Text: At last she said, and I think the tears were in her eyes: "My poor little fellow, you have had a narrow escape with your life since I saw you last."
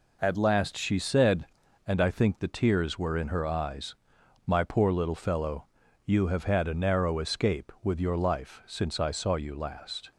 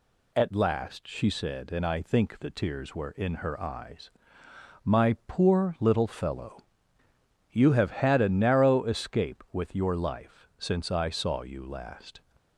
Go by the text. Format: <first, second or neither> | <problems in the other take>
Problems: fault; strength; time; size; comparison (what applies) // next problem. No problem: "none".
neither | none